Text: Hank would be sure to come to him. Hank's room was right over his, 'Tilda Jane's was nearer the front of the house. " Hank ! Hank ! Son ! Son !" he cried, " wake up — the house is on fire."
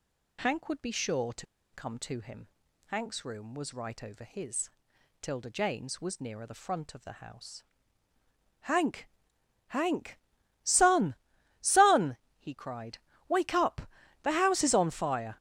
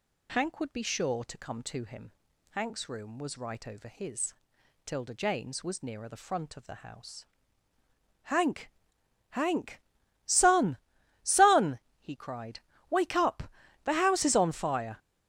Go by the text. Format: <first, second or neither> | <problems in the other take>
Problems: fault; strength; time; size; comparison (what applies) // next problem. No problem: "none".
second | pauses between "to" and "come"; slight; at 1.4 s; 0.27 s long